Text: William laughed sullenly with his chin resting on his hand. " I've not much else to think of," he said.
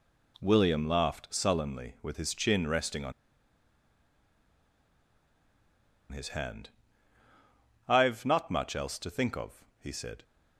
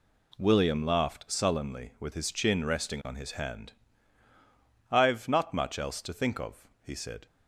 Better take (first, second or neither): second